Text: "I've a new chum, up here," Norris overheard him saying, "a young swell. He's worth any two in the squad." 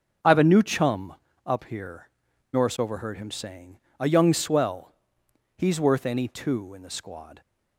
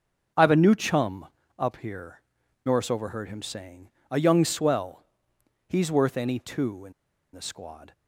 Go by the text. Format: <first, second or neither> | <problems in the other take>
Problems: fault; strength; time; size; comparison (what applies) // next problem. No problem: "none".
first | starts louder than the rest; until 1.6 s; 7 dB; also in the first // pauses between "in" and "the"; at 6.9 s; 0.41 s long